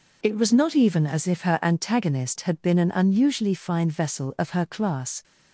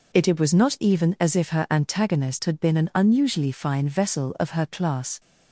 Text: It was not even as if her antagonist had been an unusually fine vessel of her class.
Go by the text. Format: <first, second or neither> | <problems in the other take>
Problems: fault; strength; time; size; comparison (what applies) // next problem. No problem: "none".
first | says "It" twice; at 0.2 s